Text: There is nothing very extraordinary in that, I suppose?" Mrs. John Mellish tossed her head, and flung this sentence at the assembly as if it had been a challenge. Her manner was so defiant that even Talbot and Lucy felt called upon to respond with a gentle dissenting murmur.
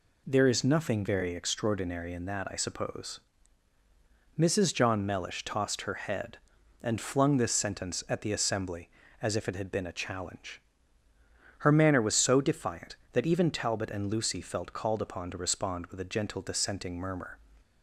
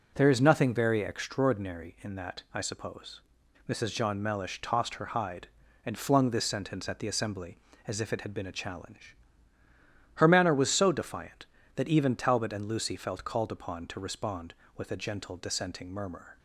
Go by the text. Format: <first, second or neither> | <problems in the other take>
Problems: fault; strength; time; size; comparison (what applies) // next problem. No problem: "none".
first | says "hide" for "head"; at 5.0 s